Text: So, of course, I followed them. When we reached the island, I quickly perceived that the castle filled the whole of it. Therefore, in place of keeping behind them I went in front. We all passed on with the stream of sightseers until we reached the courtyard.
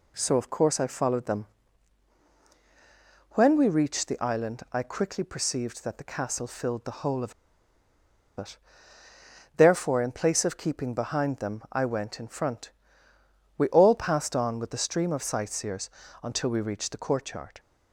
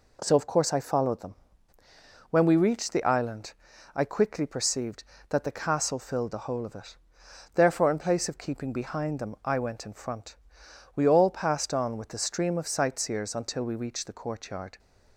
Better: second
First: pauses between "of" and "it"; at 7.3 s; 1.0 s long // pauses between "sightseers" and "until"; slight; at 15.8 s; 0.34 s long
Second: none

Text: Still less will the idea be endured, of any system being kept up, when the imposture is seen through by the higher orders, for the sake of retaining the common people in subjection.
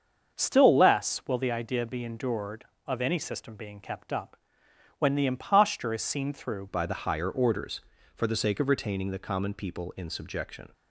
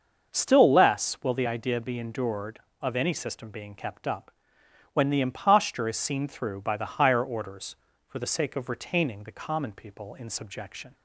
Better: second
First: starts louder than the rest; until 1.4 s; 6.5 dB // changes voice at "by"; from 6.6 s on; 4.1 s long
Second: starts louder than the rest; until 1.3 s; 6.5 dB

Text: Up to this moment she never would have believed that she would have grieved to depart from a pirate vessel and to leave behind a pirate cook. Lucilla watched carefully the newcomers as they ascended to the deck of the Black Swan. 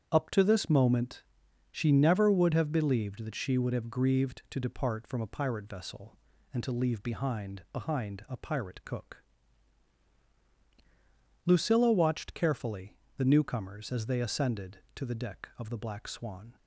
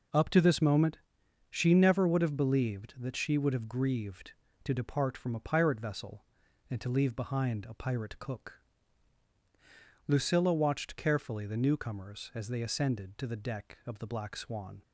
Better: second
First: starts louder than the rest; strong; until 1.1 s; 8.5 dB // pauses between "moment" and "she"; noticeable; at 1.2 s; 0.48 s long // says "behind" twice; at 7.7 s // pauses between "carefully" and "the"; slight; at 12.9 s; 0.22 s long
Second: pauses between "moment" and "she"; noticeable; at 0.9 s; 0.54 s long

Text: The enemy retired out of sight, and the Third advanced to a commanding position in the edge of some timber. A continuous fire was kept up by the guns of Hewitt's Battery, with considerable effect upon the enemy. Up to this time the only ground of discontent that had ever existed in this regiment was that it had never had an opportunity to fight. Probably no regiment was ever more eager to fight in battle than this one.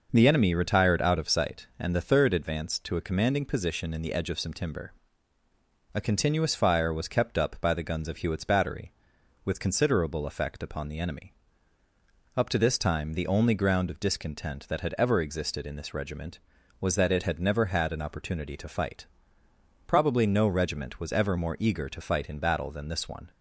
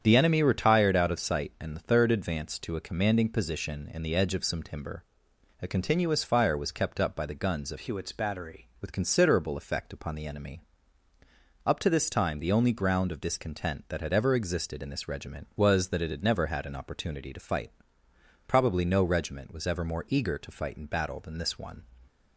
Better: first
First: none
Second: starts louder than the rest; strong; until 1.0 s; 8.5 dB // changes voice from "Hewitt's" to "Battery"; from 7.7 to 8.6 s; 0.9 s long

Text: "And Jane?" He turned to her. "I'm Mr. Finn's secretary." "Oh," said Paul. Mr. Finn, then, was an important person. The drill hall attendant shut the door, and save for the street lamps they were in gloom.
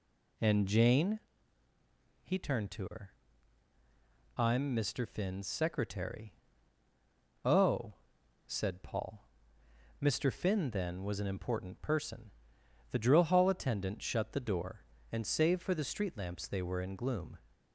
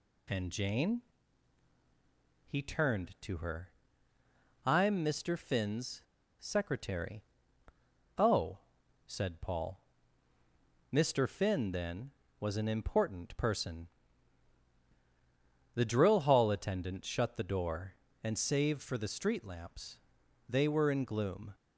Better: first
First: none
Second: pauses between "Finn's" and "secretary"; at 6.0 s; 0.36 s long // pauses between "lamps" and "they"; noticeable; at 19.9 s; 0.50 s long

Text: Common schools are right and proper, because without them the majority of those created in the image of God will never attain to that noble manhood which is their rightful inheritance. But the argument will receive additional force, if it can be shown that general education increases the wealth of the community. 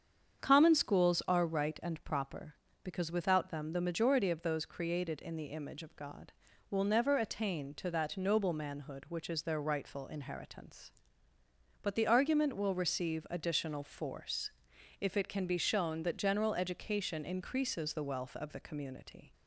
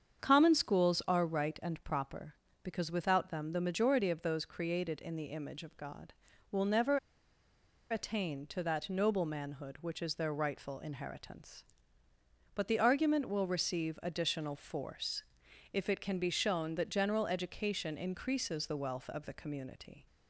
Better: first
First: starts louder than the rest; strong; until 1.4 s; 7.5 dB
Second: starts louder than the rest; strong; until 1.2 s; 7.5 dB // pauses between "never" and "attain"; noticeable; at 6.9 s; 0.92 s long

